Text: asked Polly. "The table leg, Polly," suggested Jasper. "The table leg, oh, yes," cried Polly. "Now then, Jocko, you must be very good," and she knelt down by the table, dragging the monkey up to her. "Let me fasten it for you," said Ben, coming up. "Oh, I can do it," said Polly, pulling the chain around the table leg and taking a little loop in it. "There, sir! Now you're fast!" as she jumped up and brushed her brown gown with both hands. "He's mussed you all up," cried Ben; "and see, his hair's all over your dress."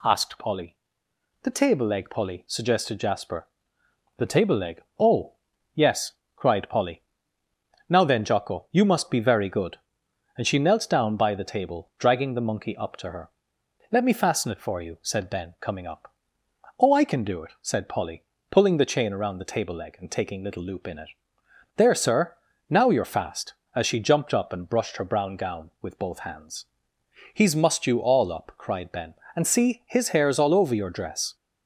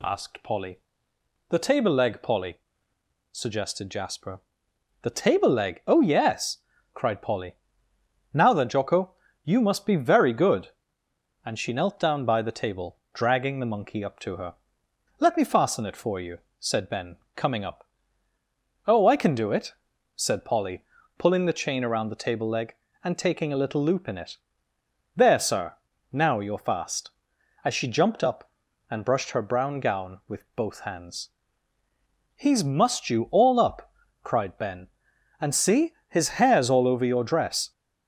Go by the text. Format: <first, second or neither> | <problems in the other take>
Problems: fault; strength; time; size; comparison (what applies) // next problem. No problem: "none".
second | skips "a"; at 20.4 s